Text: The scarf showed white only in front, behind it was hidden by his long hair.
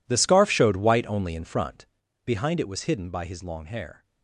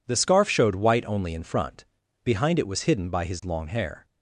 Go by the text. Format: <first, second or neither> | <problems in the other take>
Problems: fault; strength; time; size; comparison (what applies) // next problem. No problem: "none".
second | gets quieter; strong; throughout; 17.5 dB